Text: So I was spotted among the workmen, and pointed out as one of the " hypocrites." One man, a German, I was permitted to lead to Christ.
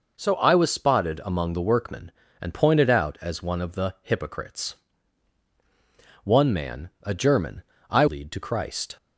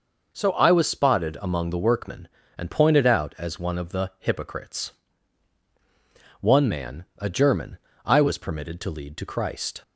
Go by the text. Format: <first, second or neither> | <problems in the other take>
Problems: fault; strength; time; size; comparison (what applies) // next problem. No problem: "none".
second | skips "was permitted to"; at 8.0 s